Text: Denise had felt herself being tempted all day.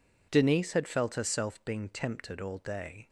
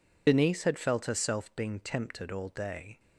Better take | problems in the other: first | loses the start of "Denise"; at 0.2 s; 60 ms

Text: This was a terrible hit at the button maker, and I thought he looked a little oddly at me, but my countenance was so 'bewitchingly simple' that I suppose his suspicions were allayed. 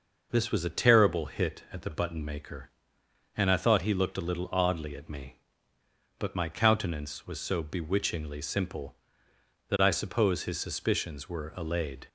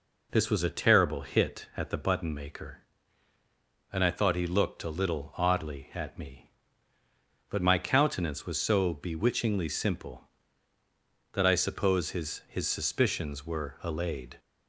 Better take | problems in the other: first | says "his" twice; at 12.4 s

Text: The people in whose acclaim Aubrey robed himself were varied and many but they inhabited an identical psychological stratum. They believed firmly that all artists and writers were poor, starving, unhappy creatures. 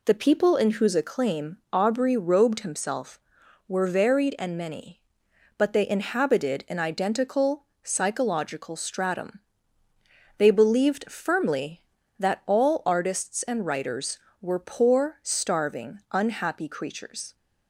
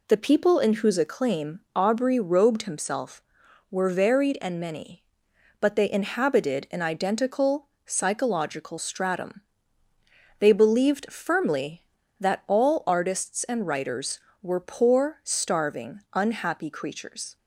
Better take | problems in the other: neither | pauses between "identical" and "psychological"; slight; the same in both

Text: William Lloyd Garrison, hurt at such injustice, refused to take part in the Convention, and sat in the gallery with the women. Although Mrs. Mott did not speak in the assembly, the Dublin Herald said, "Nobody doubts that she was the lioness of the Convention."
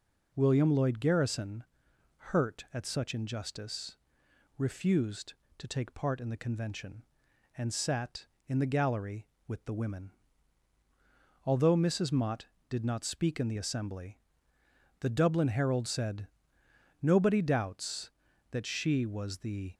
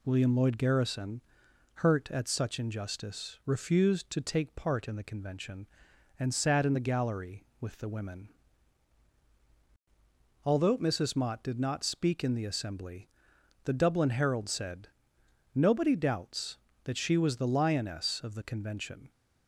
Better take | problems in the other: second | stops before "lioness of the Convention"; at 19.7 s

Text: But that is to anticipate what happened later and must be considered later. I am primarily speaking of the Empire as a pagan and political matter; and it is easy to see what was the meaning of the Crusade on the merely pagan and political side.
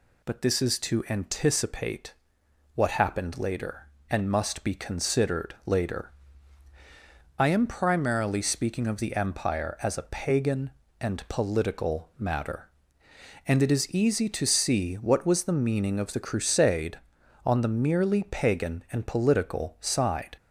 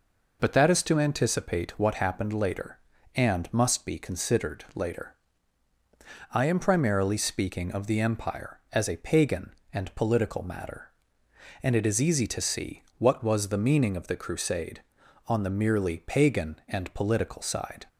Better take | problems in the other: second | says "this" for "that"; at 0.4 s // pauses between "anticipate" and "what"; noticeable; at 2.1 s; 0.60 s long

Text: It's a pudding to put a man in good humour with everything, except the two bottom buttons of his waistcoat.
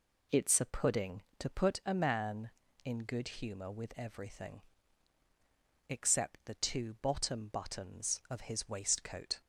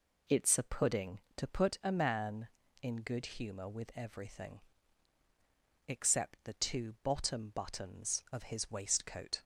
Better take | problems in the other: neither | none

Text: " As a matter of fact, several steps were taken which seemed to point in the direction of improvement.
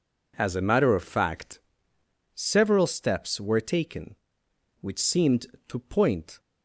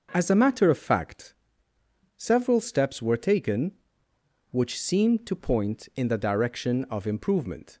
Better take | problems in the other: second | stops before "in the direction of improvement"; at 6.4 s

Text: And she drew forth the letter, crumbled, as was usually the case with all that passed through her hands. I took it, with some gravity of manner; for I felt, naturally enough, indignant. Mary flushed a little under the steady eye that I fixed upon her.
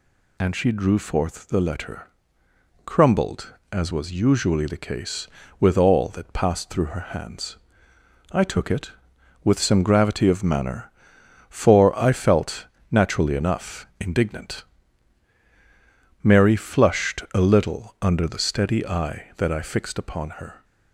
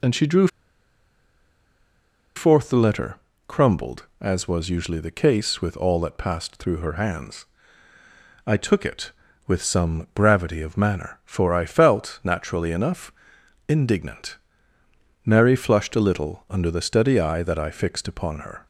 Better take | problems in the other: first | pauses between "drew" and "forth"; strong; at 0.4 s; 1.8 s long

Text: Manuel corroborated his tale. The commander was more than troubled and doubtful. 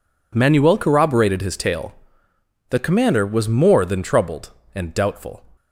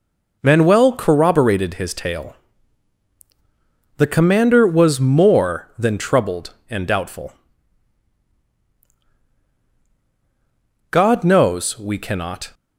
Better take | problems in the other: first | goes on to say "God knows we cannot"; from 10.9 s on; 1.6 s long

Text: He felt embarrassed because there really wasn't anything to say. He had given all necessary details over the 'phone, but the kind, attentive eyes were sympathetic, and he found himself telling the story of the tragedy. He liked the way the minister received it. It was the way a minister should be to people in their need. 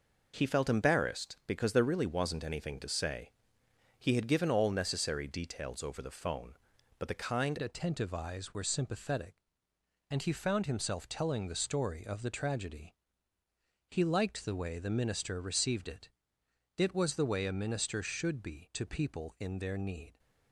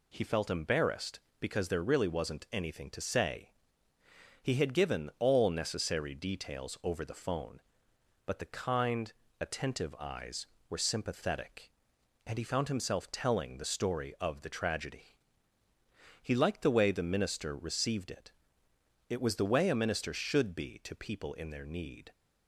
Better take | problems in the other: second | changes voice at "attentive"; from 7.6 s on; 12.5 s long

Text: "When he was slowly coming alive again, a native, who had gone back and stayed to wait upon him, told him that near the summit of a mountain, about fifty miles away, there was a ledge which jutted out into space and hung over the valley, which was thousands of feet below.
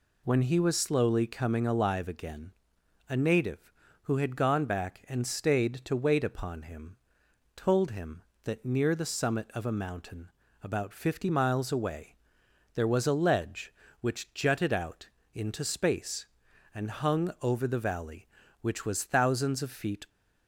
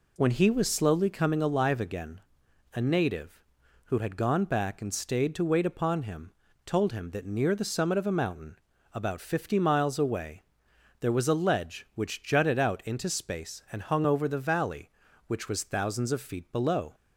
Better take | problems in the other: second | pauses between "out" and "into"; slight; at 15.0 s; 0.24 s long // stops before "below"; at 20.0 s

